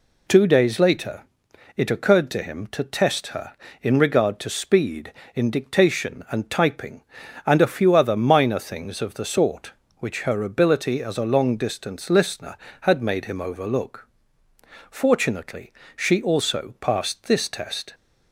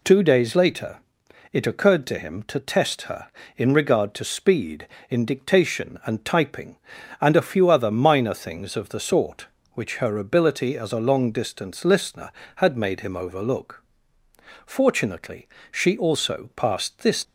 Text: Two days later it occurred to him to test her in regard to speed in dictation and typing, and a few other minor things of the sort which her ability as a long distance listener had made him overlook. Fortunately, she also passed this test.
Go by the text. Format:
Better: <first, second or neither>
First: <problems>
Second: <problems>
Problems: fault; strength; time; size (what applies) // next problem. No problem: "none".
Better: first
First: pauses between "later" and "it"; noticeable; at 1.2 s; 0.56 s long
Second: pauses between "later" and "it"; noticeable; at 0.9 s; 0.56 s long // stops before "test"; at 17.2 s